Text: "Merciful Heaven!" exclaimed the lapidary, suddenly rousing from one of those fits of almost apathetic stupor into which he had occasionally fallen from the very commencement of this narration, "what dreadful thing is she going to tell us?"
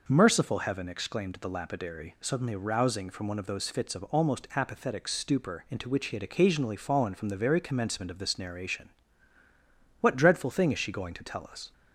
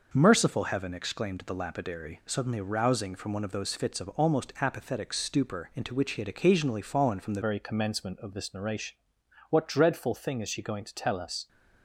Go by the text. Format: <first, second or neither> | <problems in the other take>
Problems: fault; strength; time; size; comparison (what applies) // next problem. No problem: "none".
first | changes voice at "very"; from 7.4 s on; 4.0 s long